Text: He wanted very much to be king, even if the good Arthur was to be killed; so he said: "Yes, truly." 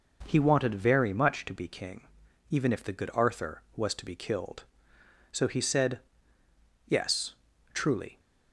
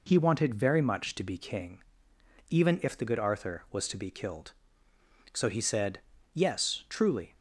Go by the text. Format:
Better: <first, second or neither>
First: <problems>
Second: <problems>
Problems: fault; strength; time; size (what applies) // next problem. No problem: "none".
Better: neither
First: none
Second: none